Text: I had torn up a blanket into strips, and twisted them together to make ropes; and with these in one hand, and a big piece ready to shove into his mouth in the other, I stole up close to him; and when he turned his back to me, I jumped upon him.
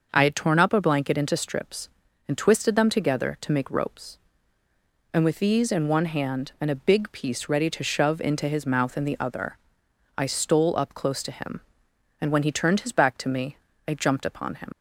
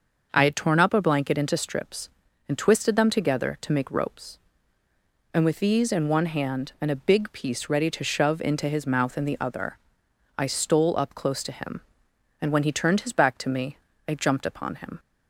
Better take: second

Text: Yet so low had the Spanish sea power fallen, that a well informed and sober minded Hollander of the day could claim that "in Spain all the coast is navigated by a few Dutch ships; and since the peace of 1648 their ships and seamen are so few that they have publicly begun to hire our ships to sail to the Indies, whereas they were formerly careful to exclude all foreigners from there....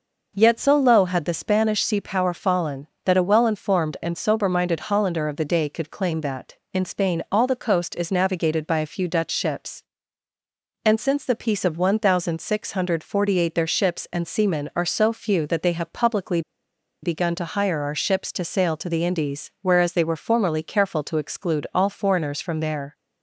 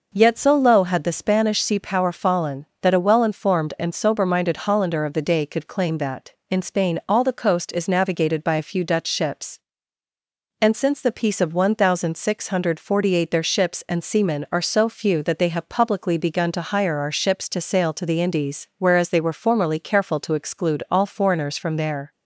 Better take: second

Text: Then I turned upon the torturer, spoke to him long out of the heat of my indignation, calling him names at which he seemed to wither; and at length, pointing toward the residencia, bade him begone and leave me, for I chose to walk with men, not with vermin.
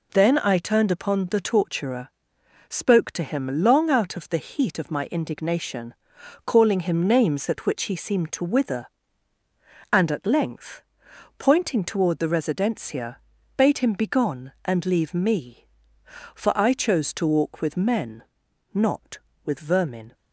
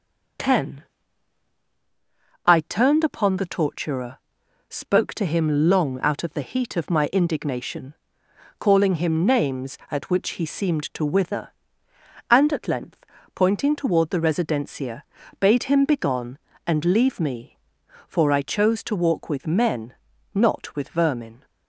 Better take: first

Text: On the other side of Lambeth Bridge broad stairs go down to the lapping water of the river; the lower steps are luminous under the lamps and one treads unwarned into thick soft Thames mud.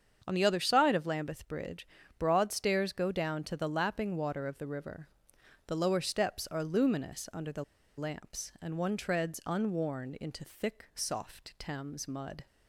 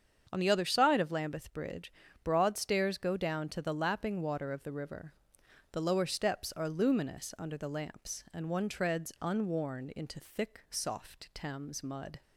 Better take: second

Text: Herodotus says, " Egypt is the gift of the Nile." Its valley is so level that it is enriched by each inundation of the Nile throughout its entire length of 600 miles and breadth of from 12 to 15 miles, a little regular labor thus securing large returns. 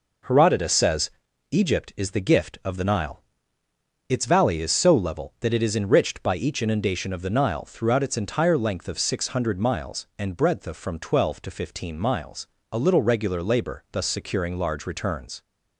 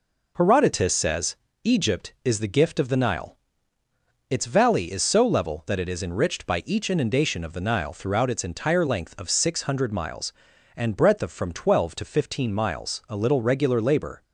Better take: first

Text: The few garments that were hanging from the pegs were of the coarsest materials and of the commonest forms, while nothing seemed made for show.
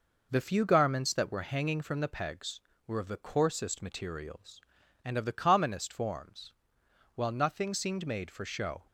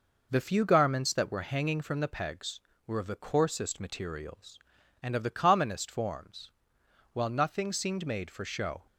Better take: neither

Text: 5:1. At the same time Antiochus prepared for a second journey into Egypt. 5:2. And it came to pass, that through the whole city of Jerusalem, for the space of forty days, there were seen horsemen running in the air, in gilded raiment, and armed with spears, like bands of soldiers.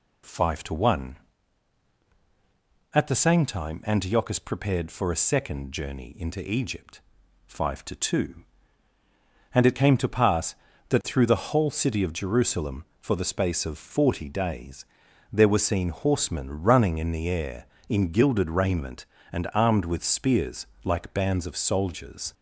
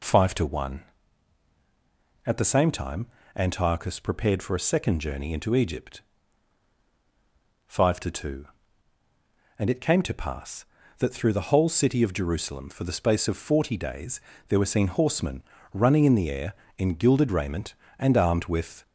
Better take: first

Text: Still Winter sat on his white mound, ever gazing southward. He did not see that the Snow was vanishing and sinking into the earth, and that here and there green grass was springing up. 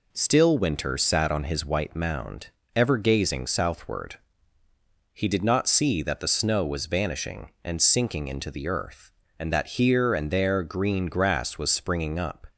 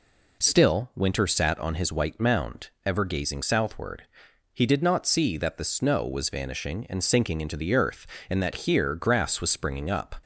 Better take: first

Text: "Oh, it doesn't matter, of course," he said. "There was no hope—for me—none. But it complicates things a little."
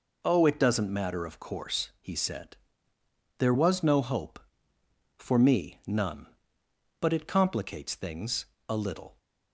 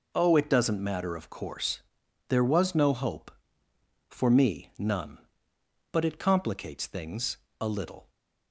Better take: first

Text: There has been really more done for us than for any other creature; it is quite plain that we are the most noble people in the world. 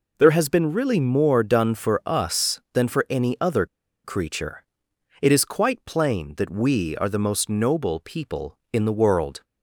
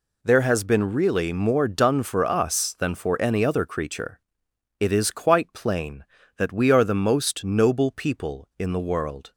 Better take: second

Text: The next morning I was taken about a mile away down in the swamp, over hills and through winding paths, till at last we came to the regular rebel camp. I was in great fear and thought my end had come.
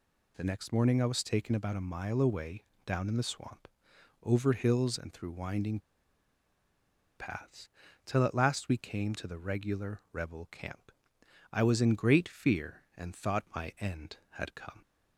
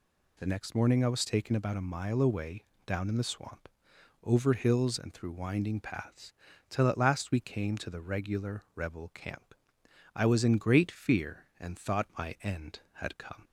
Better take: second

